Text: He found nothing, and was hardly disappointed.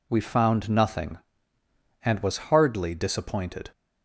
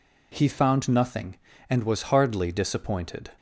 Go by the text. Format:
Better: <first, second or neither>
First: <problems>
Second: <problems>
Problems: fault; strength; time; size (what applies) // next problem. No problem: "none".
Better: second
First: says "We" for "He"; at 0.0 s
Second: none